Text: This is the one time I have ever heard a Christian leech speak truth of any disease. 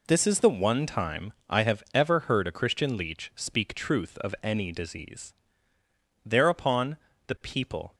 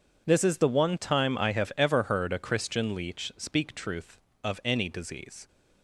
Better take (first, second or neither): second